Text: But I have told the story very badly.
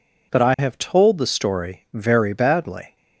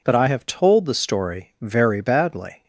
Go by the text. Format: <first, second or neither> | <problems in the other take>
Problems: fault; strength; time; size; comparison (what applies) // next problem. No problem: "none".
neither | none